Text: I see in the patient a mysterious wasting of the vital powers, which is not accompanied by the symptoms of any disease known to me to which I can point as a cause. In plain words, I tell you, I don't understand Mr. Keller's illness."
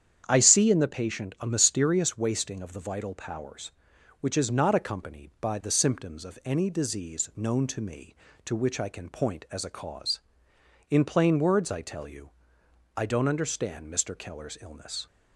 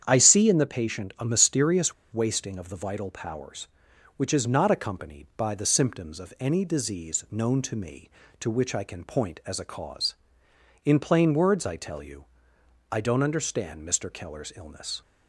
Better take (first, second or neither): first